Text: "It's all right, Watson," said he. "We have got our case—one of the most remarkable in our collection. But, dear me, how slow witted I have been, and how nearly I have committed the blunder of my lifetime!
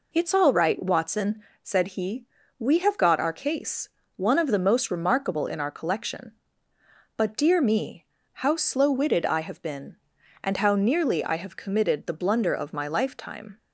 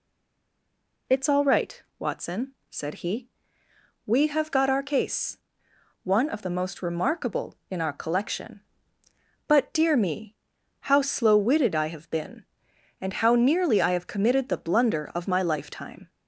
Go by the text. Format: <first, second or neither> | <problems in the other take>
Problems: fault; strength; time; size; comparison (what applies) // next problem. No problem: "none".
first | stays silent before the first word; until 1.0 s; 1.0 s long